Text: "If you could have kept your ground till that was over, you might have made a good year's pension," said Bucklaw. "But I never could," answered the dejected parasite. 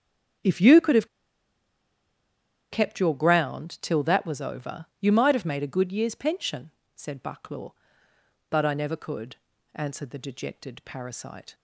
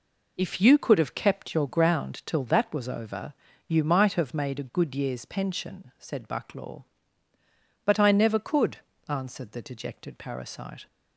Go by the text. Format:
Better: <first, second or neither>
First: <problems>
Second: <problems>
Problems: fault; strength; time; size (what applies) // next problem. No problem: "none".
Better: second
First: starts louder than the rest; strong; until 3.0 s; 7.5 dB // pauses between "have" and "kept"; strong; at 1.0 s; 1.6 s long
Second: none